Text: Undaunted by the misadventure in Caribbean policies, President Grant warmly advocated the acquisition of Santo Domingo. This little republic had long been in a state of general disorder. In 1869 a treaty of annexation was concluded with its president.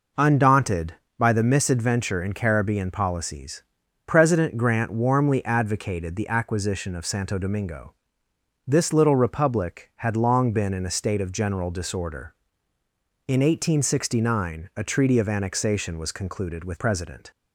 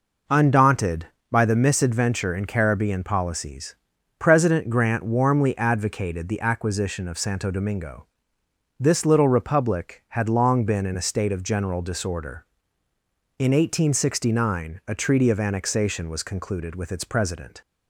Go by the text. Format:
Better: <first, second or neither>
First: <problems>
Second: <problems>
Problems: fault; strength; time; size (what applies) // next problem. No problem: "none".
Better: second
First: skips "its"; at 16.7 s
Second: none